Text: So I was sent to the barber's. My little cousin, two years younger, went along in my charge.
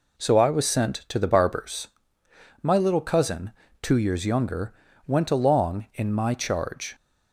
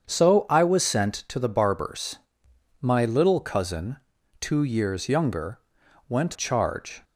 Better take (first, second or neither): first